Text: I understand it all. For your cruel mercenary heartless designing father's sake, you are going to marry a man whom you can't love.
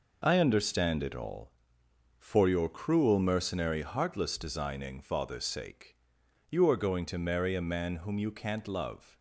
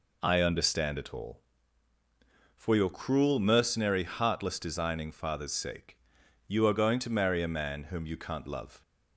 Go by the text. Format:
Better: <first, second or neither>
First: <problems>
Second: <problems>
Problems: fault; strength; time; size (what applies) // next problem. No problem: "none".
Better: second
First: gets quieter; strong; throughout; 8 dB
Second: none